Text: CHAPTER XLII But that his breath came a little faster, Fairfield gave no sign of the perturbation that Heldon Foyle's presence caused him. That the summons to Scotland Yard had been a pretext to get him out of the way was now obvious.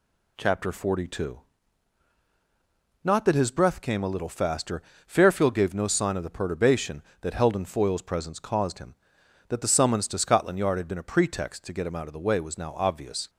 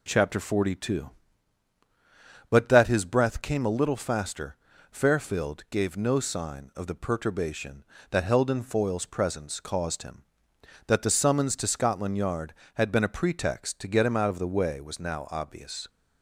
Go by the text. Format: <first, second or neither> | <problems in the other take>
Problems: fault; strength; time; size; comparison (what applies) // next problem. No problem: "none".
second | says "Not" for "But"; at 3.0 s